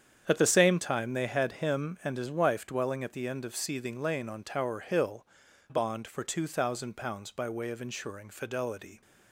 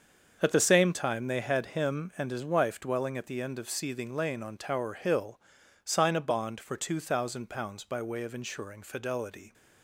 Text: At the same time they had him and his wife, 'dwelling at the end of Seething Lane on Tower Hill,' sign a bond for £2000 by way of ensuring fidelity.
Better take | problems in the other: second | starts louder than the rest; strong; until 1.2 s; 8.5 dB; also in the second // skips "sign a"; at 5.4 s

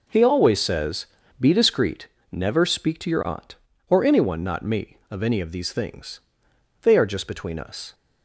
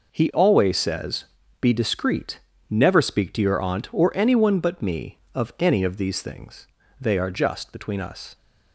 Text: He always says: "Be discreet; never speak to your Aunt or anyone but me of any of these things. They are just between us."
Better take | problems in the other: second | says "not" for "but"; at 4.4 s

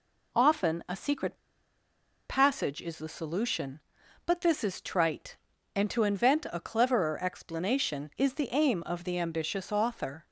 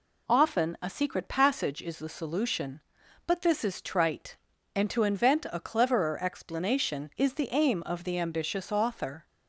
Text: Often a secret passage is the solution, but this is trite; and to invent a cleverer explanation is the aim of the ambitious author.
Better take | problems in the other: second | pauses between "secret" and "passage"; noticeable; at 1.3 s; 0.94 s long

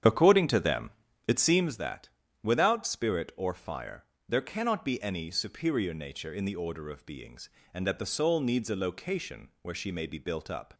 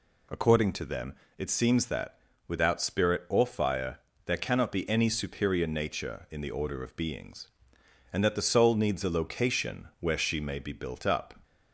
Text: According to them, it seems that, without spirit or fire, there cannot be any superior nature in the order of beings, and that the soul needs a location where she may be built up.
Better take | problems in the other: second | starts louder than the rest; strong; until 1.7 s; 8.5 dB

